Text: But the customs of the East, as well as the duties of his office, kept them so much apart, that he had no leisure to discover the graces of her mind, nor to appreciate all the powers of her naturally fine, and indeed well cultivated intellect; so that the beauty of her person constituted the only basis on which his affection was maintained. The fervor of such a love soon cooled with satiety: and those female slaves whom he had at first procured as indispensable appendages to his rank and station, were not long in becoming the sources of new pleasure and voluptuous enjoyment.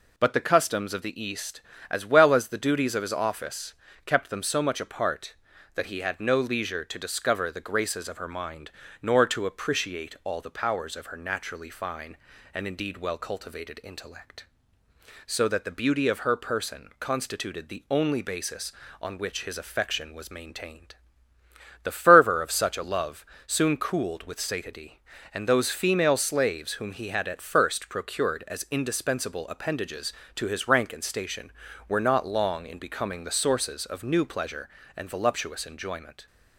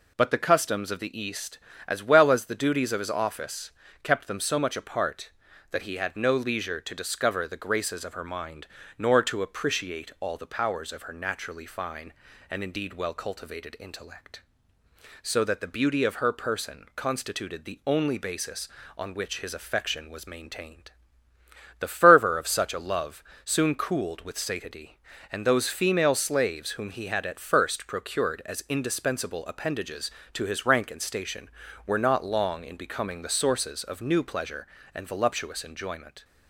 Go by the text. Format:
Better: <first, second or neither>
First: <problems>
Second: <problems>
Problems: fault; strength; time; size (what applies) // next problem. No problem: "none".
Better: neither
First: pauses between "love" and "soon"; slight; at 23.2 s; 0.22 s long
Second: pauses between "love" and "soon"; slight; at 23.2 s; 0.22 s long